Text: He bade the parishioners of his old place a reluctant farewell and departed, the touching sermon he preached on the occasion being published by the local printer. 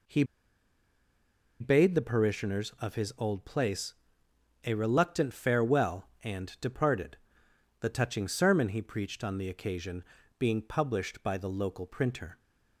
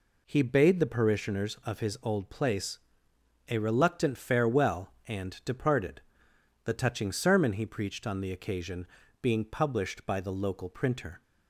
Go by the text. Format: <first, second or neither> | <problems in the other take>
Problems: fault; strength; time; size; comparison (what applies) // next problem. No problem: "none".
second | pauses between "He" and "bade"; strong; at 0.2 s; 1.3 s long // pauses between "place" and "a"; noticeable; at 3.9 s; 0.72 s long; noticeable in the second // pauses between "occasion" and "being"; slight; at 10.0 s; 0.34 s long; slight in the second